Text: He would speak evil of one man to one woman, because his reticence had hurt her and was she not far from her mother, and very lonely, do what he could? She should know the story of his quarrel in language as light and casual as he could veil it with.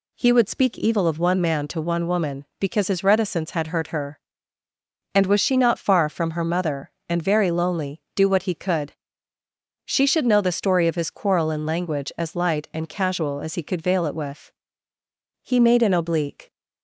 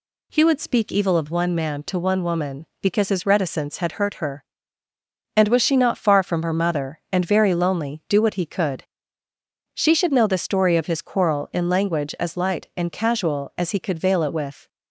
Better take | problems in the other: second | goes on to say "He made an oblique"; noticeable; from 15.4 s on; 1.0 s long

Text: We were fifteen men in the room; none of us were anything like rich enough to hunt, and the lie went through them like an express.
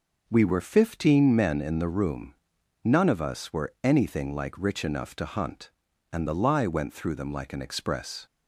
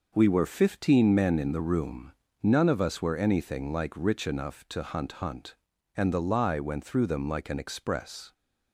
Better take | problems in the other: first | says "hunt" twice; at 5.1 s

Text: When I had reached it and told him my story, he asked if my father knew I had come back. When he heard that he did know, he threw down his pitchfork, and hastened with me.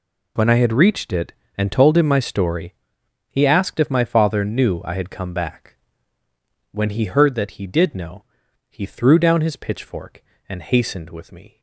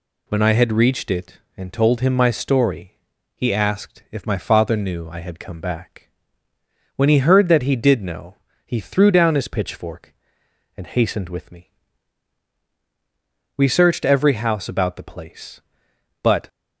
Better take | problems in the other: first | goes on to say "We searched every house about the place but"; strong; from 13.5 s on; 2.9 s long

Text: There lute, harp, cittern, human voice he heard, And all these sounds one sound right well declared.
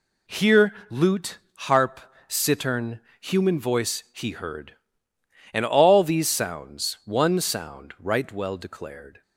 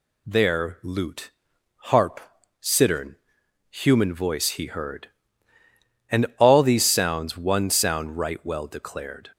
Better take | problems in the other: second | says "Here" for "There"; at 0.2 s

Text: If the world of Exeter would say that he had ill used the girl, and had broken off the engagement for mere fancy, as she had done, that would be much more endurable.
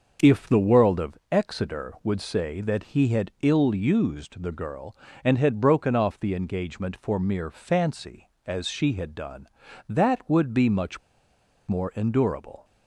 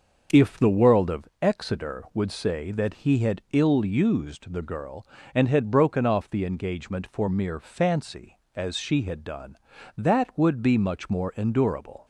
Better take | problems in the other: second | starts louder than the rest; until 1.3 s; 6.5 dB; also in the second // pauses between "much" and "more"; noticeable; at 10.9 s; 0.69 s long

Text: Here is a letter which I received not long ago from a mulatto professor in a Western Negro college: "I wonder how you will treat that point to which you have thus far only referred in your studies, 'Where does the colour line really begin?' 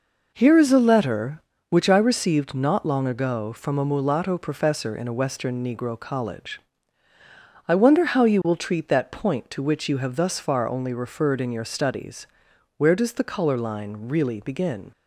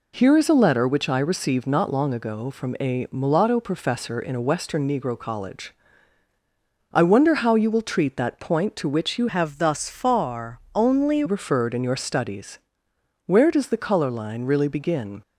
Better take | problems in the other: first | changes voice from "have" to "only"; from 9.2 to 11.2 s; 2.0 s long

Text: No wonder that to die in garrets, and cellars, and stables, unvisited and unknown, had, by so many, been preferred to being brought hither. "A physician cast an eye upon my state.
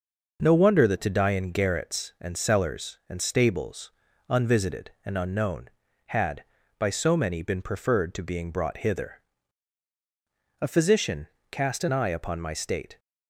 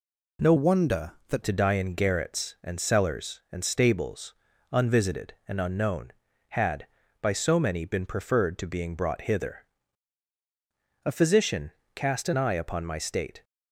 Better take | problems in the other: first | changes voice from "wonder" to "that"; from 0.5 to 1.4 s; 0.9 s long // pauses between "physician" and "cast"; slight; at 11.7 s; 0.24 s long; slight in the first

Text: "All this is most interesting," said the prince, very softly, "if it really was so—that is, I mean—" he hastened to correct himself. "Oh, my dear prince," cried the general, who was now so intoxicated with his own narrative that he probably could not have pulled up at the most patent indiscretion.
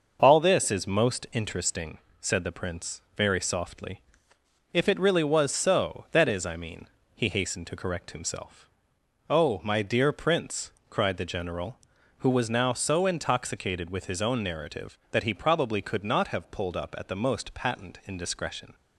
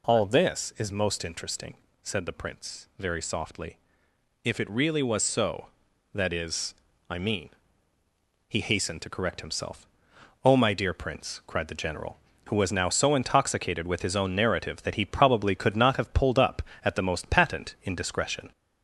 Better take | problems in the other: first | gets louder; slight; throughout; 3 dB

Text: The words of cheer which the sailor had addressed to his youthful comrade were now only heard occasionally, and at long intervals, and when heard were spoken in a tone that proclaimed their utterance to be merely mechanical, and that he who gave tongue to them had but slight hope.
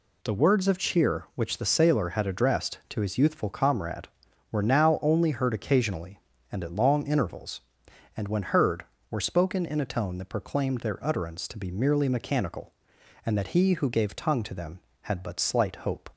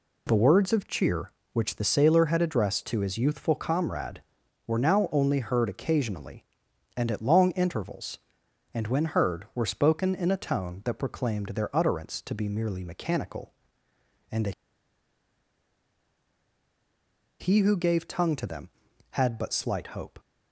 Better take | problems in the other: first | pauses between "that" and "he"; strong; at 14.5 s; 2.8 s long

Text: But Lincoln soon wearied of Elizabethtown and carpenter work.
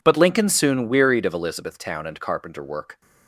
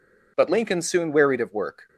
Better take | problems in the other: first | skips "Elizabethtown and carpenter"; at 1.5 s

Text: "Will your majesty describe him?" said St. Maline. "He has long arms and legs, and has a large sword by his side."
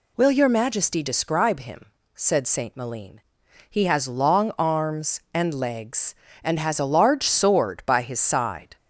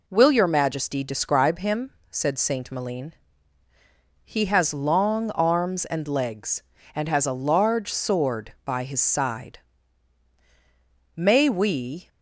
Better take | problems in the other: first | goes on to say "May we"; noticeable; from 11.1 s on; 0.92 s long

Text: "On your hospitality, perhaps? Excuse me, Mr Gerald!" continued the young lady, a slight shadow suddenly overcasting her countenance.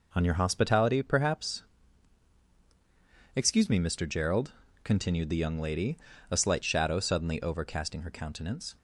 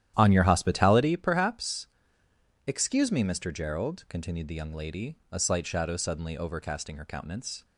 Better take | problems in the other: first | starts louder than the rest; strong; until 1.3 s; 11.5 dB

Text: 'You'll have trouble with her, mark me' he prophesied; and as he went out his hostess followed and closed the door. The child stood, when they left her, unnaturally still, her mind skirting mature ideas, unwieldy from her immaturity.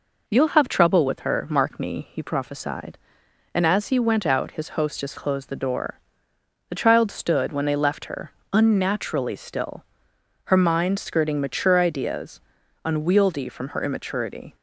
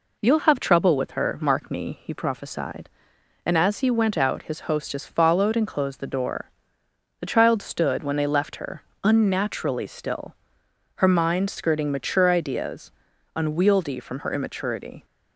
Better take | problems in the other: second | skips "followed and"; at 5.1 s

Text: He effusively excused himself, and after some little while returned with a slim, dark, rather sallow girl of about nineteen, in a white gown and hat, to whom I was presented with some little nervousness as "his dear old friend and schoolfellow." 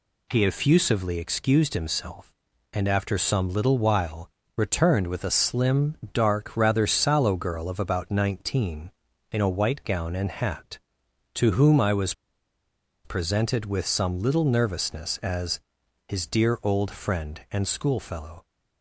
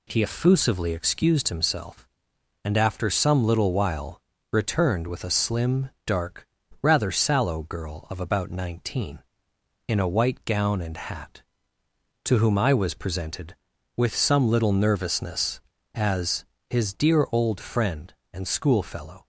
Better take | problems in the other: second | pauses between "while" and "returned"; slight; at 4.2 s; 0.28 s long; slight in the second // pauses between "was" and "presented"; noticeable; at 12.1 s; 0.92 s long // pauses between "as" and "his"; noticeable; at 15.5 s; 0.48 s long; slight in the second

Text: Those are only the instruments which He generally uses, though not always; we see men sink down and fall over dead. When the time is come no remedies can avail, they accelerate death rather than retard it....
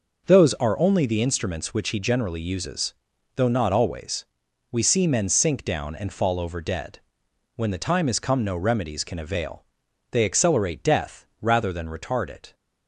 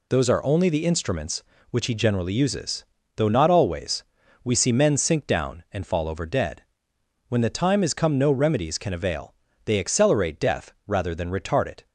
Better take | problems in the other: neither | none

